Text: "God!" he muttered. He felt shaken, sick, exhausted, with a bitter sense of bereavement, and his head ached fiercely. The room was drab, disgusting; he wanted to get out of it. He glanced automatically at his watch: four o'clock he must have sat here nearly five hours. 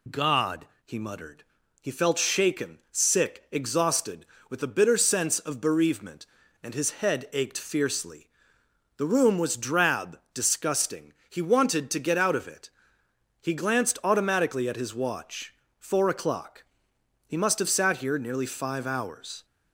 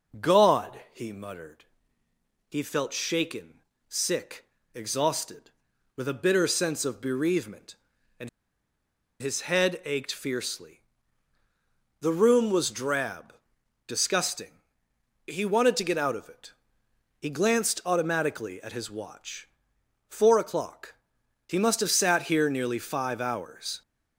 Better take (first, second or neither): first